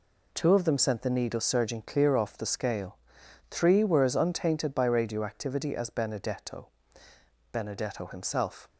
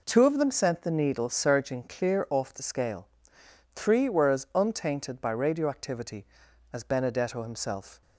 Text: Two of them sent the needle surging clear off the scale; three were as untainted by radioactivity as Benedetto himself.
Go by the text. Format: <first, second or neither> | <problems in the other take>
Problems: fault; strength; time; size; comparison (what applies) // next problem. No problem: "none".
second | says "Benedetto" twice; at 7.5 s